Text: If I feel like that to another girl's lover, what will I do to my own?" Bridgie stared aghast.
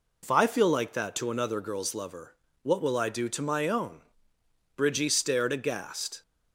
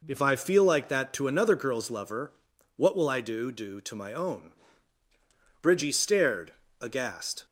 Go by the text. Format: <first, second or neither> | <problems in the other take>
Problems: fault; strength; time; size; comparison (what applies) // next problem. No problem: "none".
first | says "do" twice; at 3.5 s // pauses between "stared" and "aghast"; slight; at 6.5 s; 0.30 s long